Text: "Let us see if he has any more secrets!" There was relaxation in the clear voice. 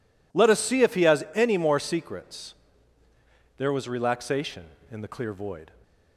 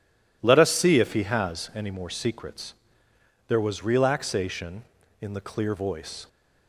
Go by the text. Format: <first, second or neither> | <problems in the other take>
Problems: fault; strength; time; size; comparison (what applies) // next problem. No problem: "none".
second | says "void" for "voice"; at 5.3 s